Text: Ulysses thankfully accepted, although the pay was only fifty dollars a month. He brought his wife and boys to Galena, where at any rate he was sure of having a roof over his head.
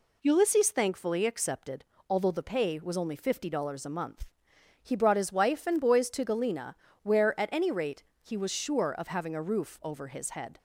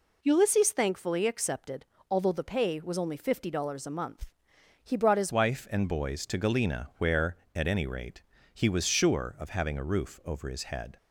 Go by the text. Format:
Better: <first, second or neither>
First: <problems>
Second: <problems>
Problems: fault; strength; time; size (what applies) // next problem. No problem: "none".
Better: first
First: pauses between "rate" and "he"; slight; at 8.0 s; 0.20 s long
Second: changes voice at "wife"; from 5.3 s on; 5.6 s long // pauses between "rate" and "he"; slight; at 8.2 s; 0.30 s long